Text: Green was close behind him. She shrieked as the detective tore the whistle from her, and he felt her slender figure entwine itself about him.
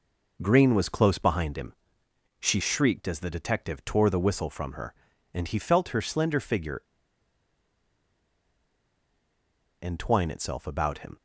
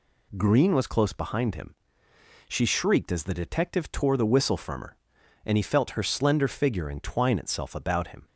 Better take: second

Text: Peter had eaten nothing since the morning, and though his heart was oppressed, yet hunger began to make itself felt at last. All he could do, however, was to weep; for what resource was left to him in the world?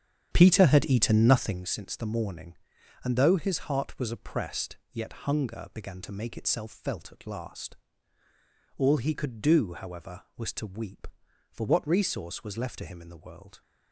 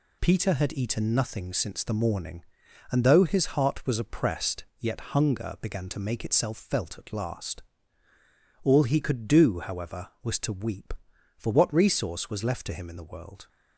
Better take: second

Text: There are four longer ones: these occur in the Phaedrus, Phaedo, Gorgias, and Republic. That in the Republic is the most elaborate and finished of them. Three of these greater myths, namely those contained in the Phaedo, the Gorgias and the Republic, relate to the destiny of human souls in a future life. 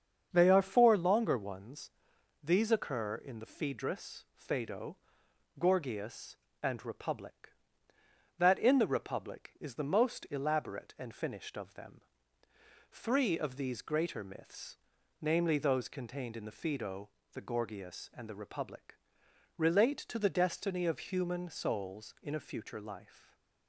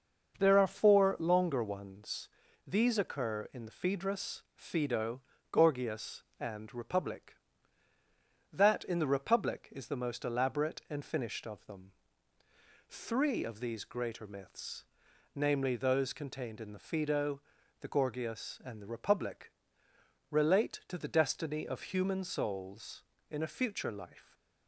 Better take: second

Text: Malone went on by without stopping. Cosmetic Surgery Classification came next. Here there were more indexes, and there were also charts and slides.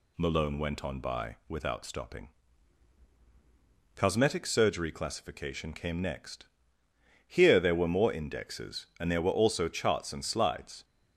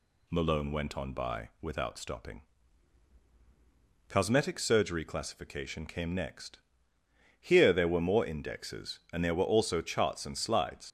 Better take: first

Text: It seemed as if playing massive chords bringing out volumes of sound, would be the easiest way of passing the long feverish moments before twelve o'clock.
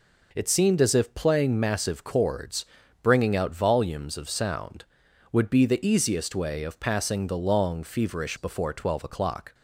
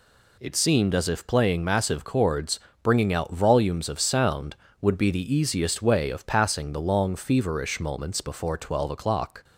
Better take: second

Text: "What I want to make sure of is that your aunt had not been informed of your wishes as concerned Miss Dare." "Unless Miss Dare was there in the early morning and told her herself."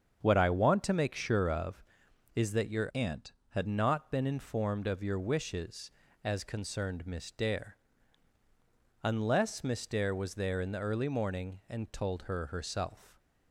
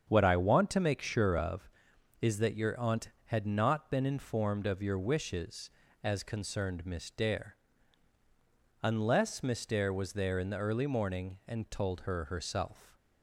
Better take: second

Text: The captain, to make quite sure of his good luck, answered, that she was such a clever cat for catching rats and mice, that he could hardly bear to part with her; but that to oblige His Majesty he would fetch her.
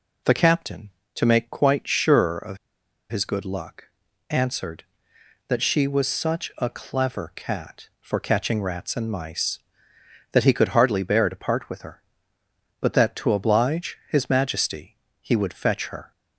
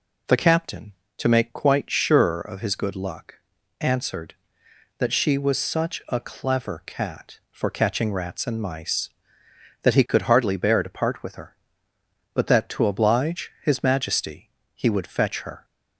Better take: second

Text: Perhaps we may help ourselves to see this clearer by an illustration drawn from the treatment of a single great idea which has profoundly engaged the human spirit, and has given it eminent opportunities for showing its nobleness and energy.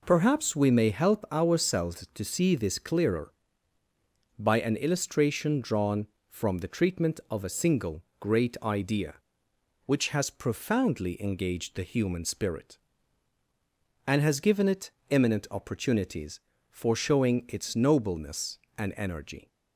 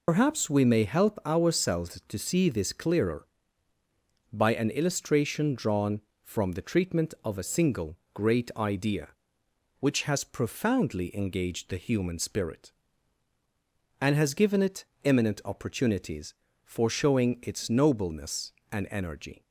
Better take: first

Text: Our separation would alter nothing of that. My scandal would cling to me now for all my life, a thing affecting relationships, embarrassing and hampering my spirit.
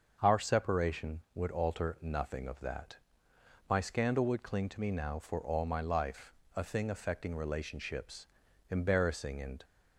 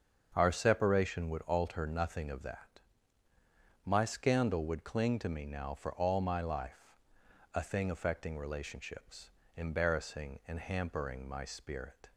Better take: second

